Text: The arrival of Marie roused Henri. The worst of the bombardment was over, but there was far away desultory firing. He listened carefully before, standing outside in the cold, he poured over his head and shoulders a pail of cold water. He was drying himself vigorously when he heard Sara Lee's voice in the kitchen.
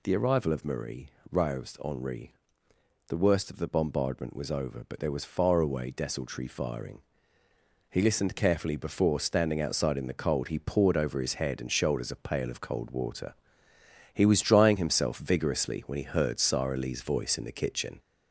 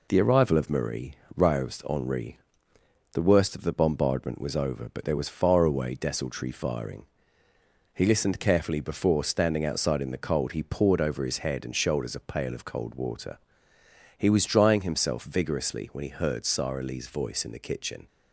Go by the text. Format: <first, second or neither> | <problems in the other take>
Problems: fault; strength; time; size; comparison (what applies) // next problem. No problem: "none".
second | gets louder; slight; throughout; 3 dB // pauses between "Marie" and "roused"; slight; at 1.0 s; 0.24 s long; slight in the second